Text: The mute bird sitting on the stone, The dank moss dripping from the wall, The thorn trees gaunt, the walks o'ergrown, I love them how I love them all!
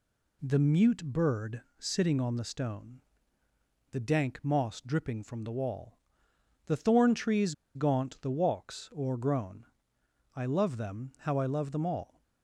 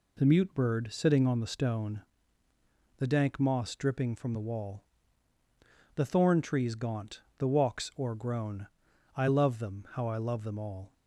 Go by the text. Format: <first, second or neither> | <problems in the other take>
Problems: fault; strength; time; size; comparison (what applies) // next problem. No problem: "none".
second | pauses between "bird" and "sitting"; slight; at 1.6 s; 0.18 s long // pauses between "trees" and "gaunt"; slight; at 7.5 s; 0.22 s long